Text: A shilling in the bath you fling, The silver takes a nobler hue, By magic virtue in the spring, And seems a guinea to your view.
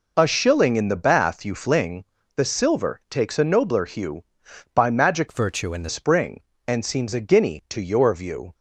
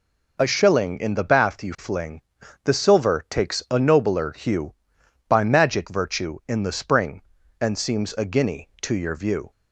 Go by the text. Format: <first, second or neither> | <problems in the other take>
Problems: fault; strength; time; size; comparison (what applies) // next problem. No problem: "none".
second | changes voice from "virtue" to "the"; from 5.2 to 5.8 s; 0.6 s long